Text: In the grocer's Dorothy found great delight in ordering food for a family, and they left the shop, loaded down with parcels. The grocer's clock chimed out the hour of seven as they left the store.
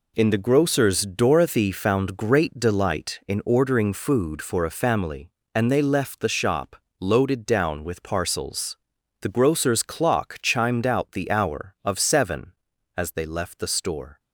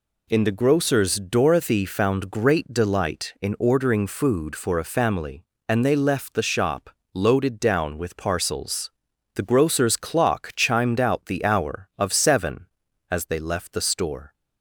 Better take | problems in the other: second | gets quieter; strong; throughout; 8.5 dB

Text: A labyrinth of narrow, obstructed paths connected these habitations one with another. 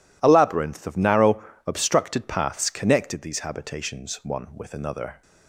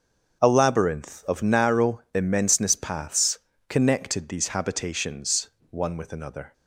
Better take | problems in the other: first | starts louder than the rest; until 1.4 s; 6.5 dB // says "immenseness" for "obstructed"; at 2.1 s // pauses between "paths" and "connected"; slight; at 3.3 s; 0.28 s long // pauses between "habitations" and "one"; slight; at 5.4 s; 0.20 s long

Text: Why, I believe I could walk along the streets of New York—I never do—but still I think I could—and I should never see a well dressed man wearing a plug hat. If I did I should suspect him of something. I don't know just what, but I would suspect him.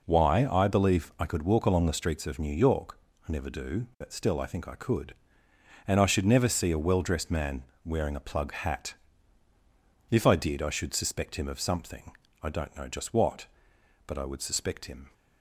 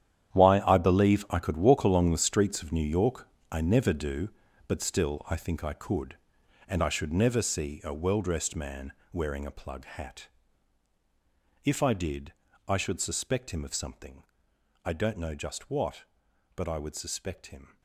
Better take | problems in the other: first | gets quieter; strong; throughout; 14.5 dB // pauses between "man" and "wearing"; slight; at 8.9 s; 0.18 s long; slight in the first // pauses between "did" and "I"; slight; at 12.3 s; 0.36 s long

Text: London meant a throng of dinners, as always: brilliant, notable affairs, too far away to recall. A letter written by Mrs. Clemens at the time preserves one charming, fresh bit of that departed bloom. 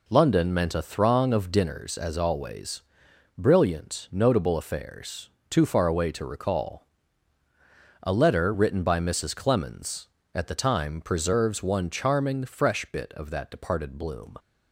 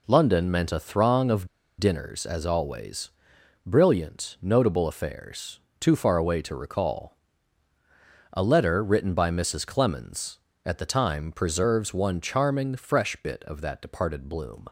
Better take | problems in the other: first | pauses between "of" and "dinners"; slight; at 1.4 s; 0.30 s long

